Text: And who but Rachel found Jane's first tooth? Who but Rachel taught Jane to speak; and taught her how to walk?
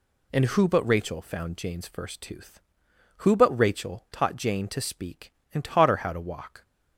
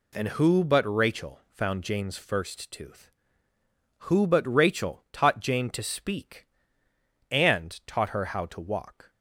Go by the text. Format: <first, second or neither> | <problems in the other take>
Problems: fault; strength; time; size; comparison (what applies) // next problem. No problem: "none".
neither | none